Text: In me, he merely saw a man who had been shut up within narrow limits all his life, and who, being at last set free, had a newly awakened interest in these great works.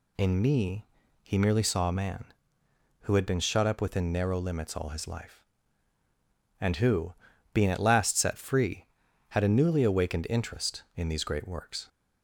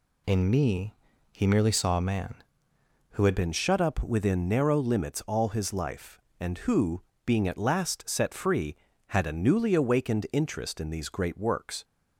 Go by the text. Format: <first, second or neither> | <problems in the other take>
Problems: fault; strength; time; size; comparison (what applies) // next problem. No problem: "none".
first | changes voice at "been"; from 3.3 s on; 8.5 s long